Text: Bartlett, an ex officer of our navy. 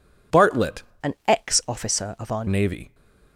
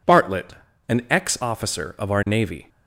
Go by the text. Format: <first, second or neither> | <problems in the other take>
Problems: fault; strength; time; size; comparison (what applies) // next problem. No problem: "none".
second | changes voice from "an" to "our"; from 1.0 to 2.4 s; 1.4 s long